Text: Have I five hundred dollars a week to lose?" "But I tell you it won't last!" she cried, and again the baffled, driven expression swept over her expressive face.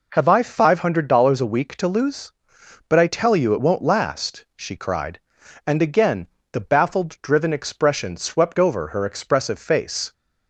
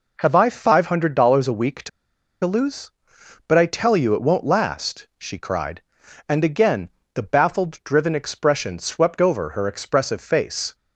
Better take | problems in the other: first | pauses between "to" and "lose"; noticeable; at 1.8 s; 0.55 s long // pauses between "again" and "the"; slight; at 6.9 s; 0.24 s long; slight in the first

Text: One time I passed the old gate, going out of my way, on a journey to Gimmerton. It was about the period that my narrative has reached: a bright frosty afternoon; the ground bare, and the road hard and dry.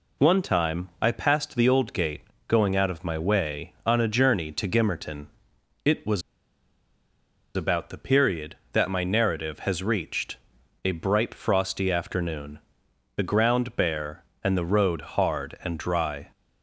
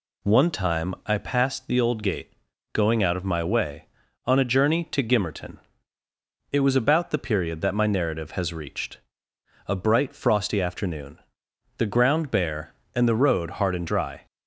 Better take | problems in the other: second | pauses between "was" and "about"; strong; at 6.2 s; 1.3 s long

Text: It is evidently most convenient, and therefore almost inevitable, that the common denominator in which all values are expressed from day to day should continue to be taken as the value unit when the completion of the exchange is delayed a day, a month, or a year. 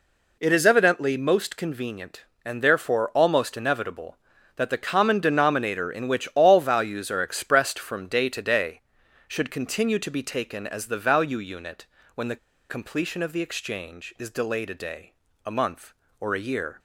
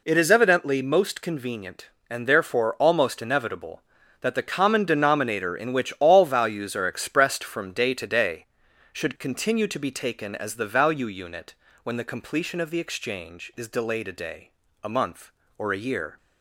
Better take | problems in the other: second | pauses between "unit" and "when"; slight; at 11.8 s; 0.28 s long; slight in the second // pauses between "the" and "completion"; slight; at 12.3 s; 0.33 s long

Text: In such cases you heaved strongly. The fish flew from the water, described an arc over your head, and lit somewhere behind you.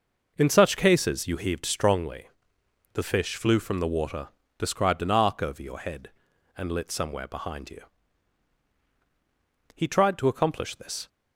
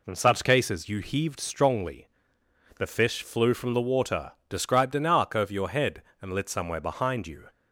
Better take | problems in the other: second | goes on to say "He tried to accomplish this"; from 9.7 s on; 1.3 s long

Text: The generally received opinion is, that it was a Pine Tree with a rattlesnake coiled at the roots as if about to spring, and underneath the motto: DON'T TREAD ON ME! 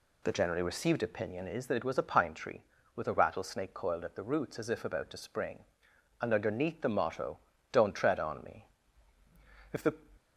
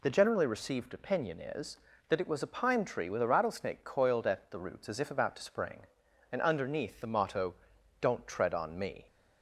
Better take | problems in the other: second | goes on to say "If the"; slight; from 9.7 s on; 0.20 s long

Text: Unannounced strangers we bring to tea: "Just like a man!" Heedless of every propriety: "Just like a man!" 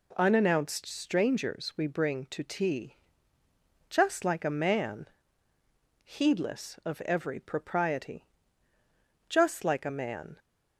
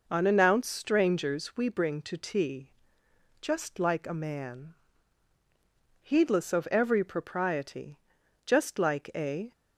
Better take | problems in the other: first | stops before "man"; at 9.5 s

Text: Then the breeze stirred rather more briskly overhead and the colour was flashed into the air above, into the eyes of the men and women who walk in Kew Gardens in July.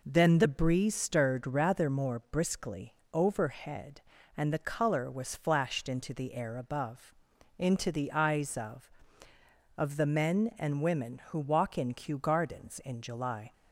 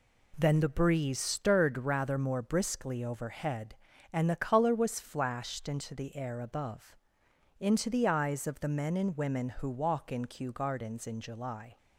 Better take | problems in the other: second | pauses between "briskly" and "overhead"; slight; at 2.9 s; 0.18 s long // says "of" twice; at 9.7 s

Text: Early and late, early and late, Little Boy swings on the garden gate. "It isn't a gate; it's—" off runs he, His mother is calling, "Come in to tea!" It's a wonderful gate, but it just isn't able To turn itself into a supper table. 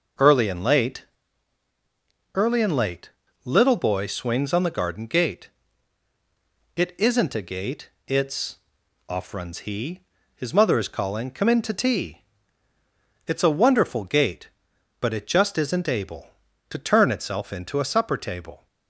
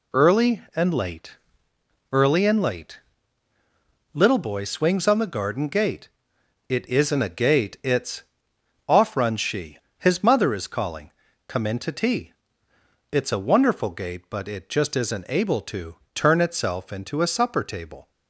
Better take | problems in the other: first | says "she" for "he"; at 9.3 s // pauses between "To" and "turn"; slight; at 15.9 s; 0.18 s long

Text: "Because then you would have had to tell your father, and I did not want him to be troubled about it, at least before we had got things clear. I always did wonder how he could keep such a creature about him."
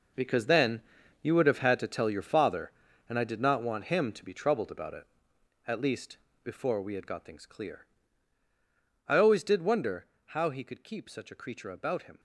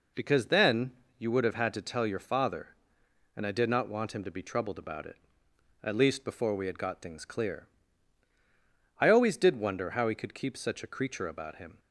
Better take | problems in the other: second | gets quieter; strong; throughout; 12.5 dB // pauses between "then" and "you"; at 0.7 s; 0.42 s long; slight in the second // pauses between "least" and "before"; slight; at 6.1 s; 0.26 s long // pauses between "wonder" and "how"; slight; at 10.0 s; 0.20 s long

